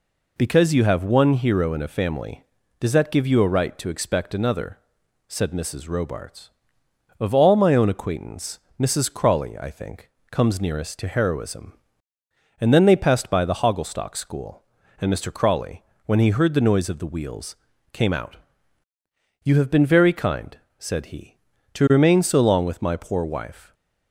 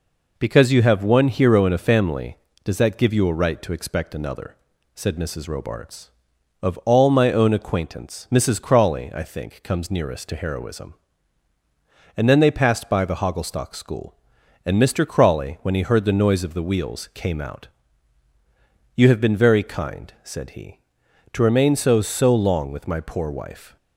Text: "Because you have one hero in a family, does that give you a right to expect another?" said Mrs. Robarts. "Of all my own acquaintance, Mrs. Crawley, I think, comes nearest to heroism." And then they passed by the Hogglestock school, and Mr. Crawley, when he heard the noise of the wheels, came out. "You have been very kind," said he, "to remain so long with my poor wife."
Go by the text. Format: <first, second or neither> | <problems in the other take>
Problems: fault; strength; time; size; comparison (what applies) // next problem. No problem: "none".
first | says "so" twice; at 22.0 s